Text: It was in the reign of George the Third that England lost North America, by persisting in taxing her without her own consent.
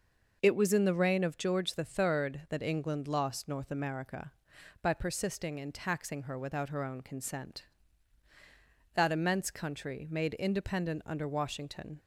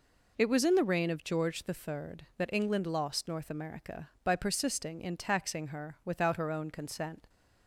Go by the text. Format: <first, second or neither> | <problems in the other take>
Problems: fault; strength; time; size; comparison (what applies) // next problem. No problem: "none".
second | goes on to say "That immense country made independent under Washington"; strong; from 8.9 s on; 3.0 s long